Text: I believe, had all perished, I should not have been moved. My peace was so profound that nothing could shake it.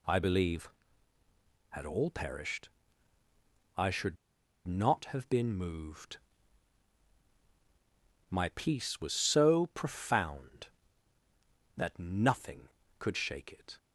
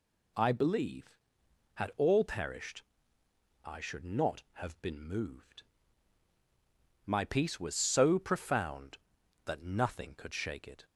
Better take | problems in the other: second | pauses between "should" and "not"; noticeable; at 4.1 s; 0.51 s long

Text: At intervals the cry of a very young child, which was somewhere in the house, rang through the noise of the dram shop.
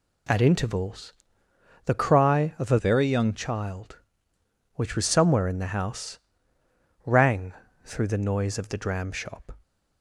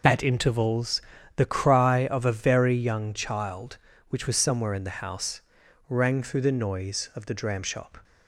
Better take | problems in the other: second | pauses between "intervals" and "the"; noticeable; at 1.1 s; 0.72 s long; slight in the second // changes voice from "very" to "young"; from 2.7 to 3.3 s; 0.6 s long // pauses between "rang" and "through"; slight; at 7.5 s; 0.32 s long

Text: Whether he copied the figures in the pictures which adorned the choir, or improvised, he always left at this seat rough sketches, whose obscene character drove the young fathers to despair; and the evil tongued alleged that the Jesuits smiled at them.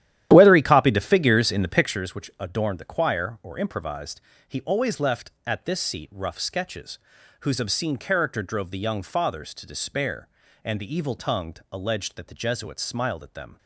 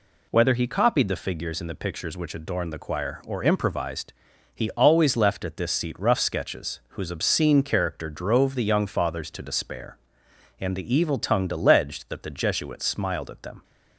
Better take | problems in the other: second | starts louder than the rest; strong; until 2.0 s; 12 dB

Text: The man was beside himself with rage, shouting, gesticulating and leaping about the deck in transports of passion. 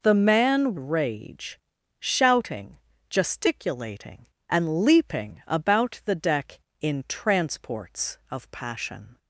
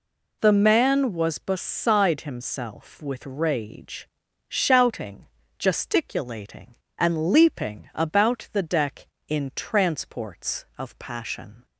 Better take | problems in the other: second | skips "was beside himself with"; at 0.7 s

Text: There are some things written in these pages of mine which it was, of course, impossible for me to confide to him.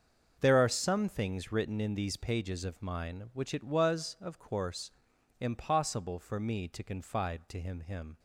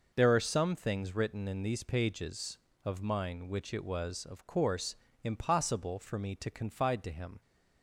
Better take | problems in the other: second | starts louder than the rest; until 1.4 s; 6.5 dB // says "him" twice; at 7.8 s

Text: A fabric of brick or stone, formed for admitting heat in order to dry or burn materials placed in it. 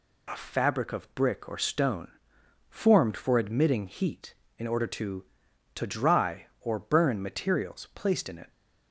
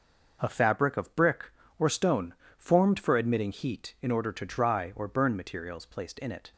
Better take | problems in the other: second | says "to" twice; at 5.7 s

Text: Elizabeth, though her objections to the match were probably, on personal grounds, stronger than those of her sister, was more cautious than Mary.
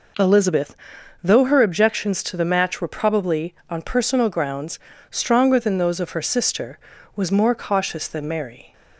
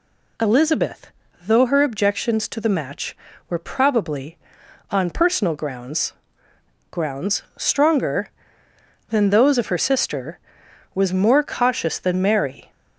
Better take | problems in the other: first | says "grounds" twice; at 6.9 s

